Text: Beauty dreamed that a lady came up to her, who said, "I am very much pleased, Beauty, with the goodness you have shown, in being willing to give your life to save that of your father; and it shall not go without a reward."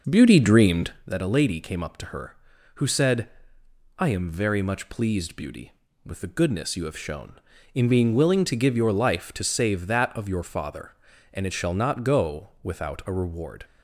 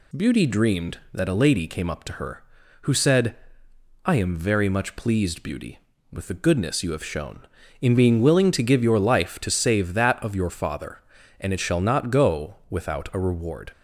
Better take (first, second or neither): second